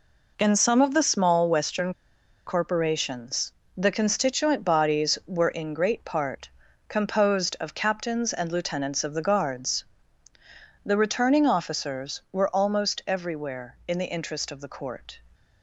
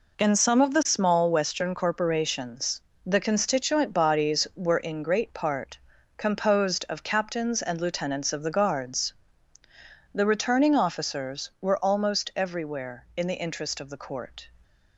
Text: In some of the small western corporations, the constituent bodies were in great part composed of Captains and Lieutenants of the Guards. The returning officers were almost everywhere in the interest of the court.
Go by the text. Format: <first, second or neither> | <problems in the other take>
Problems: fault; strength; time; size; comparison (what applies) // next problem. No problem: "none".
second | pauses between "western" and "corporations"; noticeable; at 1.9 s; 0.53 s long // pauses between "part" and "composed"; at 6.4 s; 0.40 s long; also in the second